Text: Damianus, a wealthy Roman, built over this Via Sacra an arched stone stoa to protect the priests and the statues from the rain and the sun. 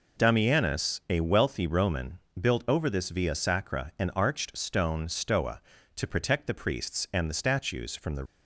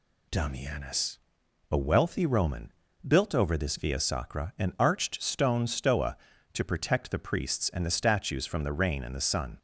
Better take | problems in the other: second | stops before "rain and the sun"; at 8.2 s

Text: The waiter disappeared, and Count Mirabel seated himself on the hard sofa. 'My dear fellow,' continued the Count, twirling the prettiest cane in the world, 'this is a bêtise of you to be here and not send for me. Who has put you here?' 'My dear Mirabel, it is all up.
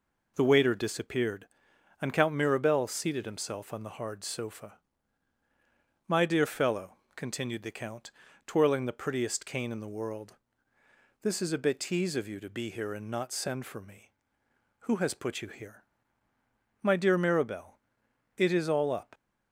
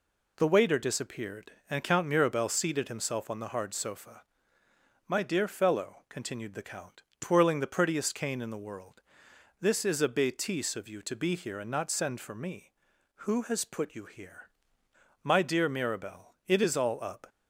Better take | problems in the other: neither | none

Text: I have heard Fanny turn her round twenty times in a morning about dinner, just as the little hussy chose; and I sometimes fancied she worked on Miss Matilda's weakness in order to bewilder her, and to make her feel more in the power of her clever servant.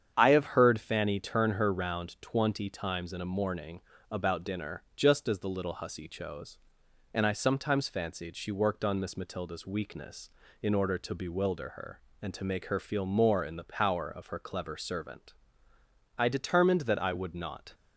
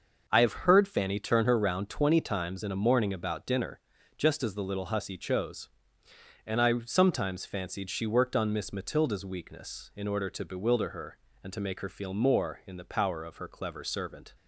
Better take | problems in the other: second | starts louder than the rest; strong; until 1.1 s; 8 dB // pauses between "morning" and "about"; slight; at 3.8 s; 0.30 s long // goes on to say "I determined that I would not"; from 16.1 s on; 1.5 s long

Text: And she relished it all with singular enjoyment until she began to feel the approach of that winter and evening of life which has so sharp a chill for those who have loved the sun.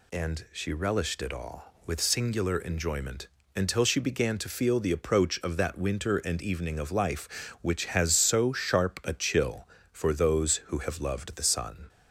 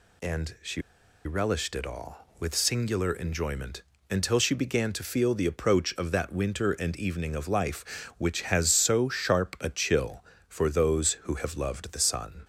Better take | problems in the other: first | pauses between "she" and "relished"; at 0.8 s; 0.43 s long // pauses between "enjoyment" and "until"; slight; at 3.8 s; 0.28 s long; slight in the first

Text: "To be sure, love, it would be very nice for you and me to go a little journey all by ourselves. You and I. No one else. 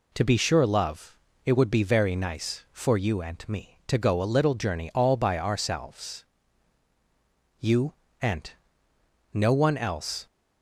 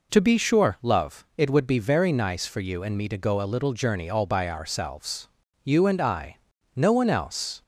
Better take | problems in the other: second | skips "I"; at 8.9 s

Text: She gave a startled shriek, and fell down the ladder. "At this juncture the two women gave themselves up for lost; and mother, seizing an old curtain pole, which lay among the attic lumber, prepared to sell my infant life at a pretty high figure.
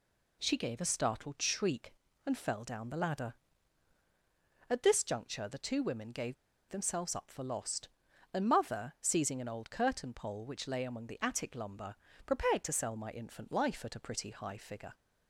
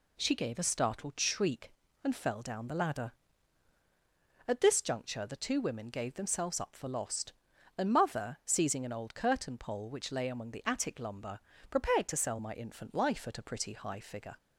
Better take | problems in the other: second | pauses between "gave" and "themselves"; slight; at 6.3 s; 0.35 s long

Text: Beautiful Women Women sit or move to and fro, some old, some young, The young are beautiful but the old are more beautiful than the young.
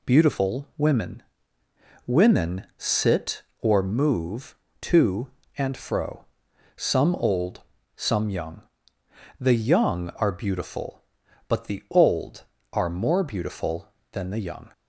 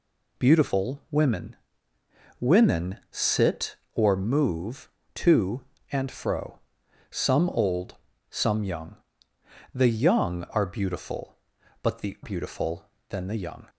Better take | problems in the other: first | pauses between "Women" and "Women"; noticeable; at 1.5 s; 0.86 s long; noticeable in the first // skips "old are more"; at 12.1 s

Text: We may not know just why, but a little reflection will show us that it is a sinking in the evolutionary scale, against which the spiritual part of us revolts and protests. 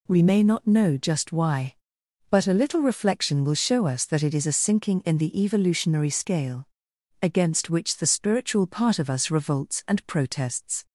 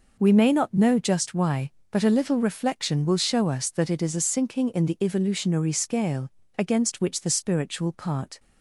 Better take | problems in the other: first | stops before "of us revolts and protests"; at 8.3 s

